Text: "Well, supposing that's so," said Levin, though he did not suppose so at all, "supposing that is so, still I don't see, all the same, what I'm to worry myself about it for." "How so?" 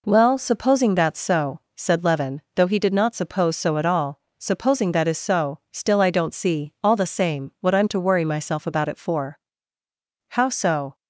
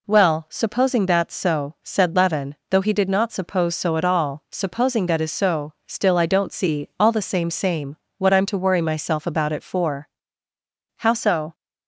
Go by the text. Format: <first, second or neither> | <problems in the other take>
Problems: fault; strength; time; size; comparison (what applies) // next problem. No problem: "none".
first | says "same" twice; at 7.5 s